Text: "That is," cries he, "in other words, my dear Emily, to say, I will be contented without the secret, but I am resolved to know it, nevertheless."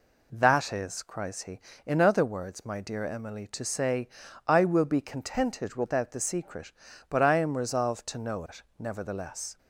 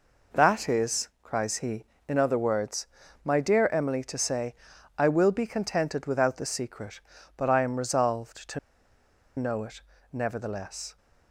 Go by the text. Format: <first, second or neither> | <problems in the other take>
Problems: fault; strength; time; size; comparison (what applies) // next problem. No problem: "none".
first | pauses between "to" and "know"; noticeable; at 8.5 s; 0.77 s long